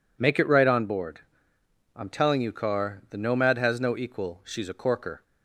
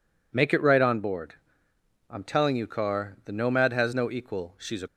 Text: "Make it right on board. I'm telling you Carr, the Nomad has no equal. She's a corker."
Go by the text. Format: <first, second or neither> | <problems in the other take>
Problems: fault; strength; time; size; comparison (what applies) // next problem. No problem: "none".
first | stops before "corker"; at 4.8 s